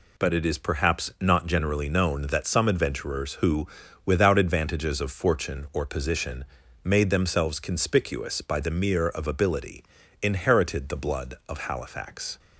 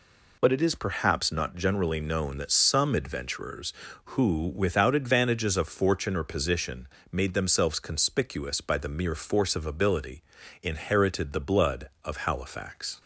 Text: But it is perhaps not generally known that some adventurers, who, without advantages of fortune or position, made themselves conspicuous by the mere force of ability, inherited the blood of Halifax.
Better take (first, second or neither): second